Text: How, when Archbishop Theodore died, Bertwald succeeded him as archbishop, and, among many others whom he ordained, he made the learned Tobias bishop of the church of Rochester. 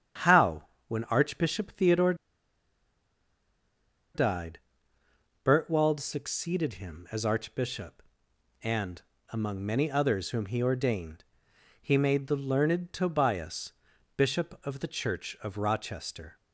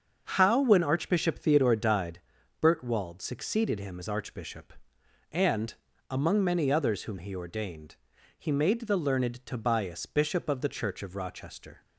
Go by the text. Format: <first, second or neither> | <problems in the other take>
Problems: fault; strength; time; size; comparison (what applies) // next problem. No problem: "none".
second | starts louder than the rest; strong; until 1.4 s; 9 dB; also in the second // pauses between "Theodore" and "died"; strong; at 2.1 s; 2.0 s long // pauses between "Tobias" and "bishop"; at 13.7 s; 0.44 s long